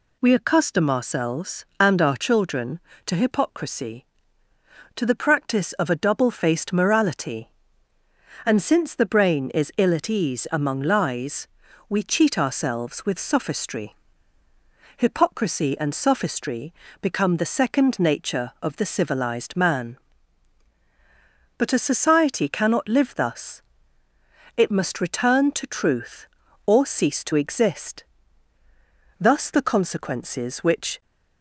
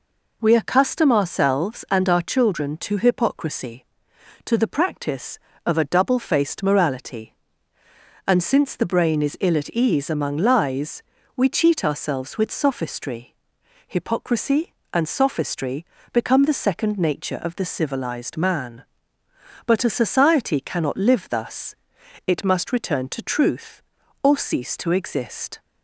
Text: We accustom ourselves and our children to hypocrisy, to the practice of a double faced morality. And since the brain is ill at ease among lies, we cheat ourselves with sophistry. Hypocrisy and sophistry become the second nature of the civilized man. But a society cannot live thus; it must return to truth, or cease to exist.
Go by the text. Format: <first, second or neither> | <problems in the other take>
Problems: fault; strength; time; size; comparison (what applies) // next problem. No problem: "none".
second | pauses between "sophistry" and "become"; slight; at 16.7 s; 0.26 s long; slight in the second // goes on to say "Thus the consequences which"; strong; from 29.2 s on; 1.8 s long